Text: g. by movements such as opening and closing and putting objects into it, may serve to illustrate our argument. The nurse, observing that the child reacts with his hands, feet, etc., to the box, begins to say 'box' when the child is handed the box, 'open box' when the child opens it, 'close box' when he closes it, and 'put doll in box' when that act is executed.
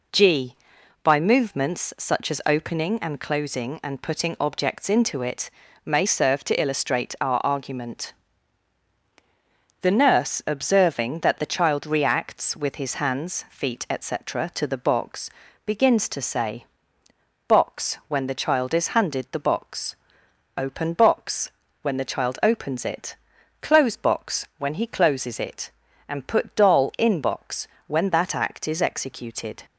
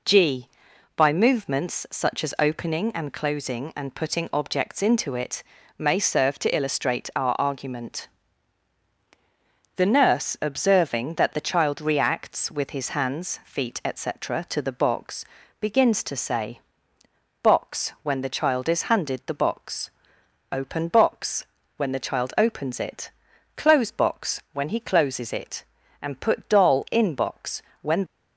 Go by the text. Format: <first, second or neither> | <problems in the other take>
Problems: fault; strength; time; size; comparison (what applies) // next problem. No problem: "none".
first | pauses between "say" and "box"; noticeable; at 16.5 s; 0.82 s long; noticeable in the first // pauses between "box" and "when"; slight; at 21.4 s; 0.32 s long; slight in the first // pauses between "box" and "when"; slight; at 27.6 s; 0.20 s long; slight in the first // stops before "that act is executed"; at 28.0 s